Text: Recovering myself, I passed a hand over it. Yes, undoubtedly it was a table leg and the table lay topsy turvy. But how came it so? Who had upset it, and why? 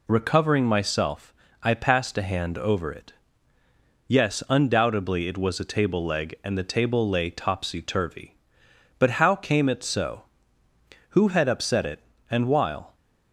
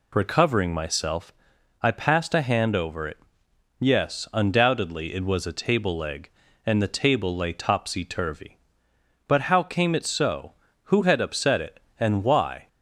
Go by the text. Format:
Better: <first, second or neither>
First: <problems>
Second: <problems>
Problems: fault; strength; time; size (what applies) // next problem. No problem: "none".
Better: second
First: says "while" for "why"; at 12.4 s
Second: none